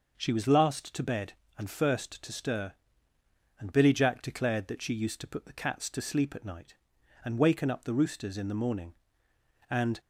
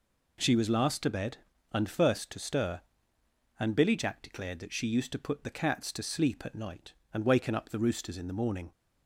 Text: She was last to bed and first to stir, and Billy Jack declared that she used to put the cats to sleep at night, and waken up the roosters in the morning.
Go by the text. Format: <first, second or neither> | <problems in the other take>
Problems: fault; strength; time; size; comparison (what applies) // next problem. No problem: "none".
second | goes on to say "And"; slight; from 9.6 s on; 0.30 s long